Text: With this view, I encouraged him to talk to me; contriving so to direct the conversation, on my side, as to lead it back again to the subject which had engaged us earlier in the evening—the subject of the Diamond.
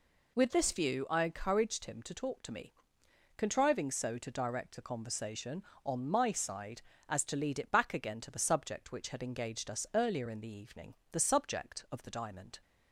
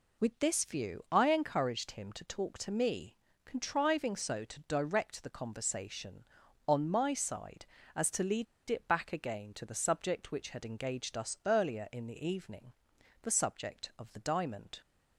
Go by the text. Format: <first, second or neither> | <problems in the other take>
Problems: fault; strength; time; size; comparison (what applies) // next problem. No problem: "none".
first | pauses between "lead" and "it"; slight; at 8.4 s; 0.25 s long